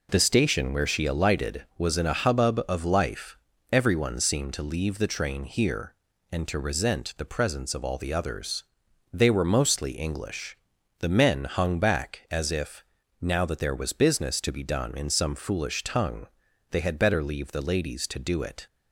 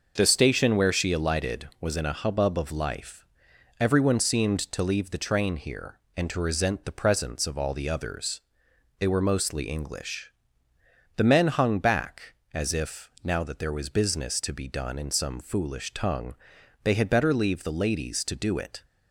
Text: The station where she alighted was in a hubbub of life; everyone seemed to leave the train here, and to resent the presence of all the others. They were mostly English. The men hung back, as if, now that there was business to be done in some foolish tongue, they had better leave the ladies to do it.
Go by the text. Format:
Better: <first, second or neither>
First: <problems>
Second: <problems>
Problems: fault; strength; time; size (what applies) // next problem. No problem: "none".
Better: neither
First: none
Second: none